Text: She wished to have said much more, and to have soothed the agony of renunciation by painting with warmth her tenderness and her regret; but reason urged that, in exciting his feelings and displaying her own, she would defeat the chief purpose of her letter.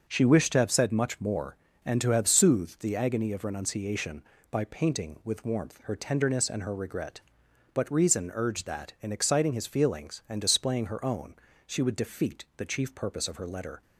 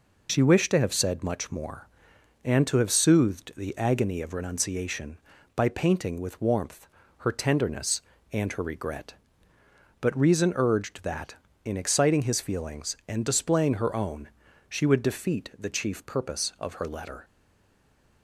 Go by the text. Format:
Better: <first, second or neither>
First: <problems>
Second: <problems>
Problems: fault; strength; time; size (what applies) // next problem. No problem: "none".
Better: first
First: none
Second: pauses between "warmth" and "her"; at 6.8 s; 0.40 s long // stays silent after the last word; from 17.2 s on; 1.0 s long